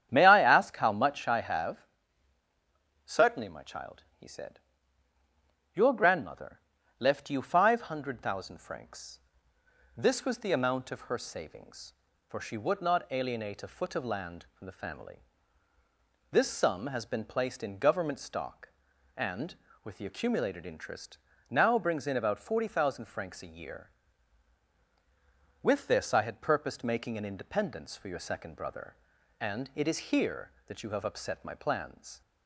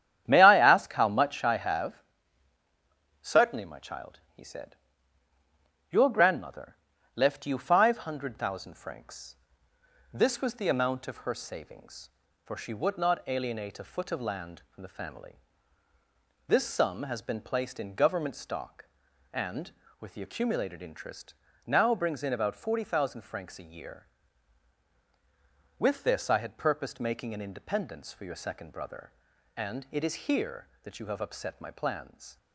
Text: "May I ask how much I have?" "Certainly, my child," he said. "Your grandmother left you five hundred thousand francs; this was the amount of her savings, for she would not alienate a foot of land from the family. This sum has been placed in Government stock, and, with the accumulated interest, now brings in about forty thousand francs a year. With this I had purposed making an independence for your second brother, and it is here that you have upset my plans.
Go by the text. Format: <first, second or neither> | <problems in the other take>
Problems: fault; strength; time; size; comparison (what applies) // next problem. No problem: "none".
first | gets quieter; throughout; 7 dB // starts louder than the rest; strong; until 1.2 s; 10 dB; strong in the first // pauses between "grandmother" and "left"; at 6.7 s; 0.38 s long; also in the first